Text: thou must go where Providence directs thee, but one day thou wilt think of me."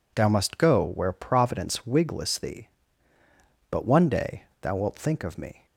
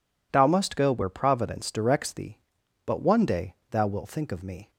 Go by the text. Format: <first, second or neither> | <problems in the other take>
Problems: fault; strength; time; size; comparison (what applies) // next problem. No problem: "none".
second | says "wigless" for "directs"; at 1.8 s // pauses between "day" and "thou"; slight; at 4.4 s; 0.18 s long; slight in the second